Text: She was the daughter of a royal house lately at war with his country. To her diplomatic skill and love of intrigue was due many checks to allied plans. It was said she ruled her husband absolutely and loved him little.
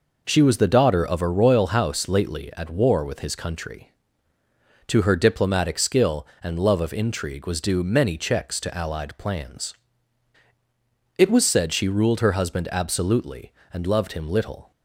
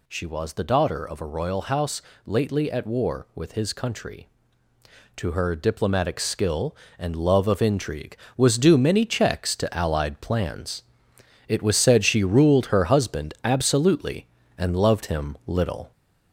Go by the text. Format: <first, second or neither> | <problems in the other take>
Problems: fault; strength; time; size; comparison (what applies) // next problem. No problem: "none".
first | gets louder; slight; throughout; 3.5 dB // pauses between "house" and "lately"; slight; at 2.0 s; 0.24 s long